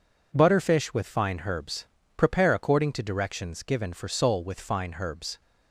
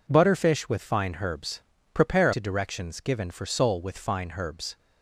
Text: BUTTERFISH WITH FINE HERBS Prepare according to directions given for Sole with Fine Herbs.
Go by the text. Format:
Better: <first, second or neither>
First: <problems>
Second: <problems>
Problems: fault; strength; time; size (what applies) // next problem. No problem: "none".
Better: first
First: pauses between "HERBS" and "Prepare"; slight; at 1.8 s; 0.28 s long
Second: pauses between "HERBS" and "Prepare"; slight; at 1.6 s; 0.30 s long // skips "according"; at 2.3 s